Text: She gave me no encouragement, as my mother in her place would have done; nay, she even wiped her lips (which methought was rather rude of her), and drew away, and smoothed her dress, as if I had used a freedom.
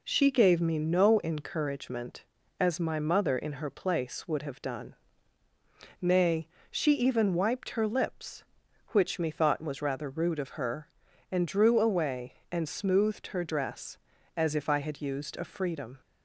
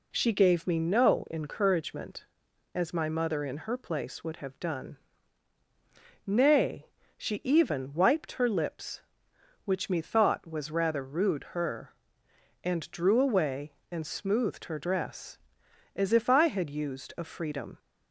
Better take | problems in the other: first | skips "of"; at 11.5 s

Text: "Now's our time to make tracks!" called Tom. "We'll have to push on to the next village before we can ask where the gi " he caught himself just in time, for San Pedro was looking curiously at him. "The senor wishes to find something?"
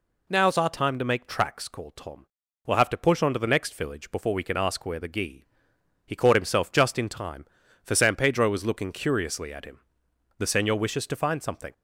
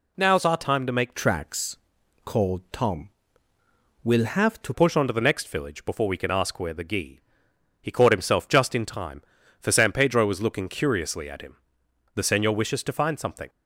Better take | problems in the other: first | changes voice from "tracks" to "to"; from 1.1 to 4.7 s; 3.6 s long

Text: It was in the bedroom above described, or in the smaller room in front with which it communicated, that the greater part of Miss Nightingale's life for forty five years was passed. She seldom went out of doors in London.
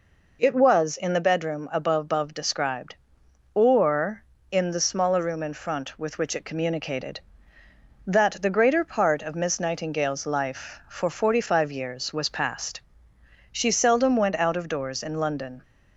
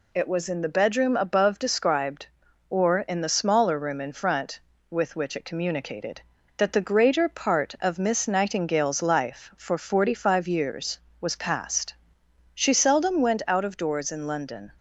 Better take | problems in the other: second | says "above" twice; at 2.0 s

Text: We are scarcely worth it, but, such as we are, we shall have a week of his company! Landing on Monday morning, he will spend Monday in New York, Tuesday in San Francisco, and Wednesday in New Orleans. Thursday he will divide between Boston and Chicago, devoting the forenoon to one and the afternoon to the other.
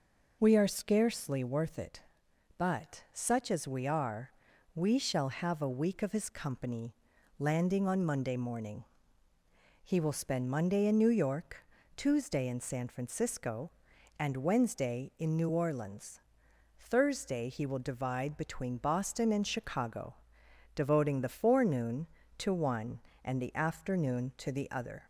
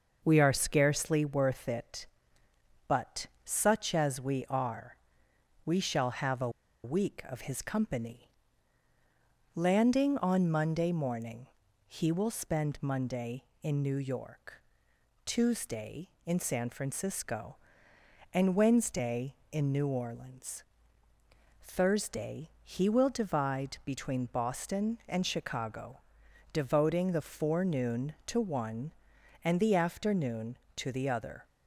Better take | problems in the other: first | pauses between "a" and "week"; slight; at 6.4 s; 0.34 s long

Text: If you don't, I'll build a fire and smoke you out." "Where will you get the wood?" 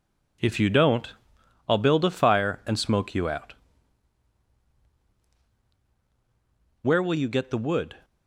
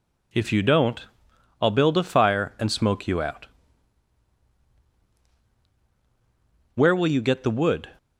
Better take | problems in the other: second | gets quieter; noticeable; throughout; 6 dB

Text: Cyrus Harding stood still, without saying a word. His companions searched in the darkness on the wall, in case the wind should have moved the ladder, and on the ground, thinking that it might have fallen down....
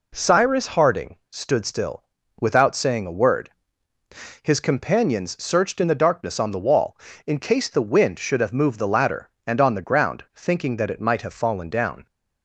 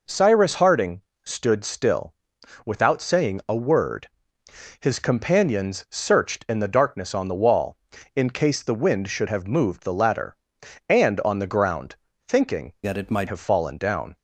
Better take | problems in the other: first | pauses between "Harding" and "stood"; slight; at 1.0 s; 0.24 s long; slight in the first // changes voice from "that" to "might"; from 12.8 to 13.2 s; 0.4 s long

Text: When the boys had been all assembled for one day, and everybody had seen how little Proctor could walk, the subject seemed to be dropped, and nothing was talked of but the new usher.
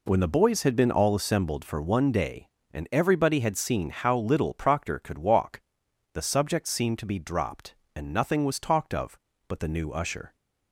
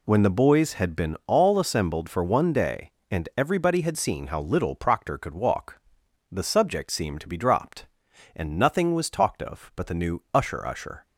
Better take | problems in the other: first | says "usher" twice; at 10.6 s

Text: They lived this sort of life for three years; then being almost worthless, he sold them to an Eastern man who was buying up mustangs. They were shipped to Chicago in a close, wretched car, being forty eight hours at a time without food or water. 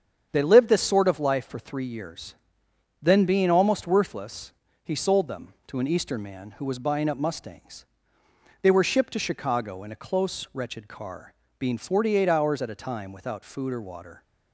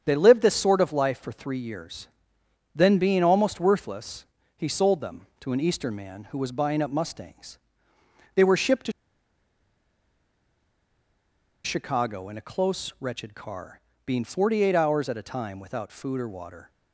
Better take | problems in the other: first | starts louder than the rest; strong; until 1.0 s; 8 dB; strong in the first // pauses between "to" and "Chicago"; strong; at 8.9 s; 2.7 s long

